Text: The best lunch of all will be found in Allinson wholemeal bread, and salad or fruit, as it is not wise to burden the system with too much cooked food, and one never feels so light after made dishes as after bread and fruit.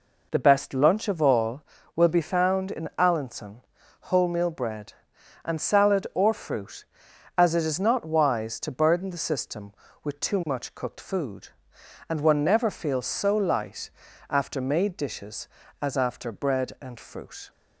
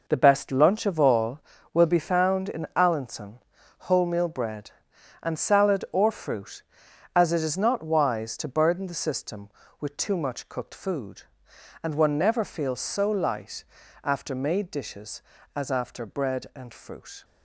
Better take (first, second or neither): first